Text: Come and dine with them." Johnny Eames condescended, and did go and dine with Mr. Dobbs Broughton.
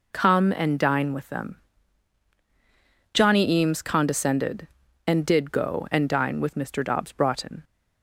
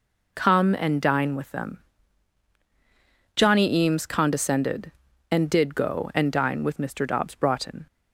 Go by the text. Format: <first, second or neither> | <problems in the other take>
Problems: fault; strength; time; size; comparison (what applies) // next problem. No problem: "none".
neither | none